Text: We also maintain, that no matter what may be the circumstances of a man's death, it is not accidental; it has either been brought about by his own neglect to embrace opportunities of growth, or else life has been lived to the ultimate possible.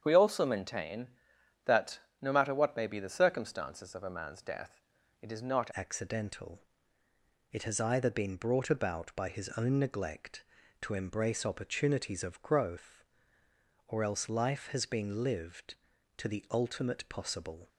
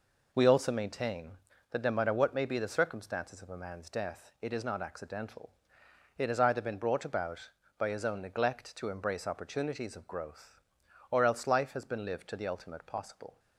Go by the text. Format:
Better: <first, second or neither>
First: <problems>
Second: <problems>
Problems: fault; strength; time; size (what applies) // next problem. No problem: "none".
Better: second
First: starts louder than the rest; strong; until 1.0 s; 7.5 dB // pauses between "that" and "no"; slight; at 2.0 s; 0.20 s long // changes voice at "accidental"; from 5.7 s on; 11.9 s long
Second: none